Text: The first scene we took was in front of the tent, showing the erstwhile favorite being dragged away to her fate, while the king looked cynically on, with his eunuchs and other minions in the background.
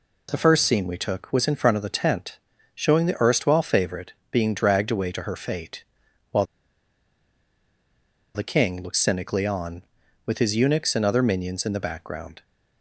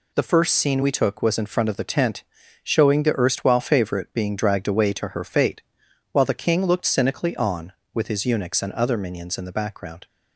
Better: second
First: pauses between "favorite" and "being"; slight; at 4.1 s; 0.16 s long // pauses between "while" and "the"; strong; at 6.4 s; 1.8 s long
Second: none

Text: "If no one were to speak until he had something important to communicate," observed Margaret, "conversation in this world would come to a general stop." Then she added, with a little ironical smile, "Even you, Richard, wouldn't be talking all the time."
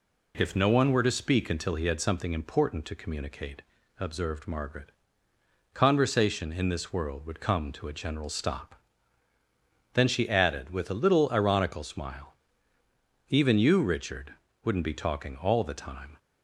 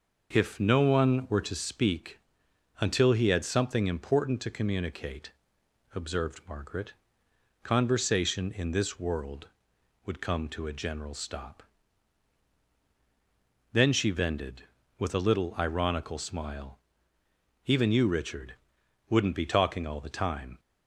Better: first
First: none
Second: pauses between "speak" and "until"; noticeable; at 2.1 s; 0.60 s long // says "vended" for "added"; at 14.0 s

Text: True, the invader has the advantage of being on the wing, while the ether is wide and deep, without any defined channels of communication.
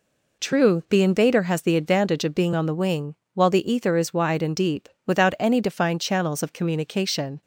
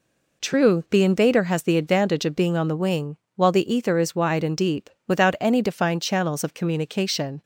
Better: neither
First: none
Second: none

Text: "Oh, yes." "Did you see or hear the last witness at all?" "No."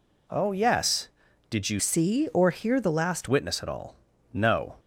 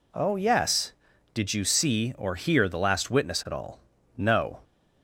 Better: second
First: changes voice from "see" to "last"; from 1.7 to 3.2 s; 1.5 s long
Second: none

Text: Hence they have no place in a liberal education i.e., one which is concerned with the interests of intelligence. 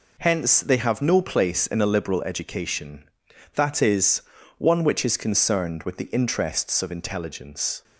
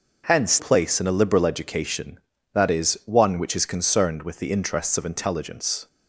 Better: first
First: none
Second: skips "they have no"; at 0.5 s

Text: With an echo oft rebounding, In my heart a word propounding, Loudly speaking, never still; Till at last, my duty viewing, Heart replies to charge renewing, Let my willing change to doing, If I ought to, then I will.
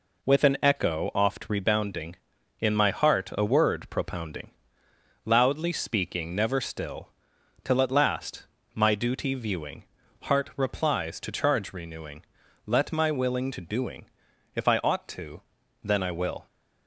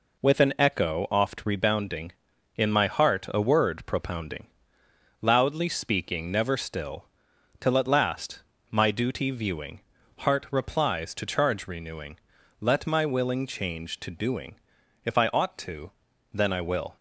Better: second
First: skips "change"; at 13.5 s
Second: none

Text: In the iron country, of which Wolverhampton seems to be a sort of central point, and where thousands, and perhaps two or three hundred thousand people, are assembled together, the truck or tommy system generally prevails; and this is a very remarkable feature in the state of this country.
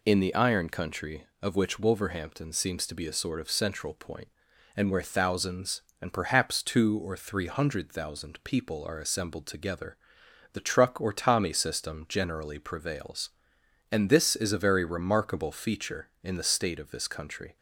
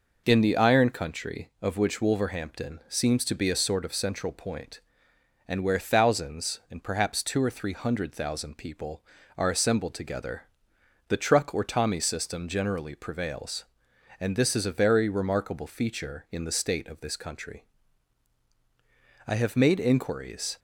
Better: first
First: none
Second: goes on to say "I have made inquiries"; from 19.2 s on; 1.3 s long

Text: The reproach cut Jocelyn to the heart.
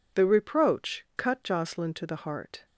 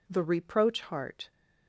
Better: first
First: none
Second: skips "cut Jocelyn to the"; at 0.8 s

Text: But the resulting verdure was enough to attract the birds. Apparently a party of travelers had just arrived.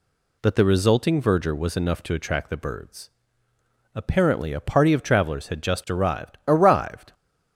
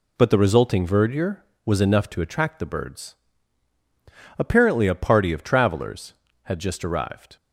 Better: second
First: says "arrived" twice; at 6.4 s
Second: none

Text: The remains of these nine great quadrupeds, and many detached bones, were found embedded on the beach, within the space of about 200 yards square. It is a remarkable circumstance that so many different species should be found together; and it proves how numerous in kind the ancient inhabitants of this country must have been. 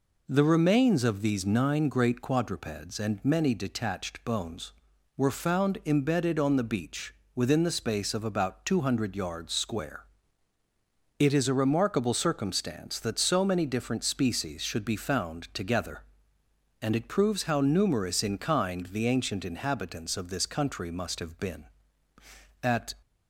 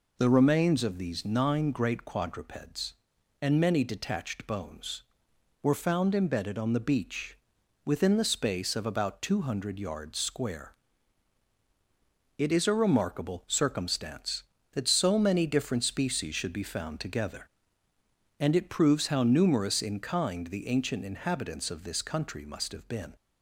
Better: second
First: goes on to say "At"; slight; from 22.6 s on; 0.32 s long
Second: none

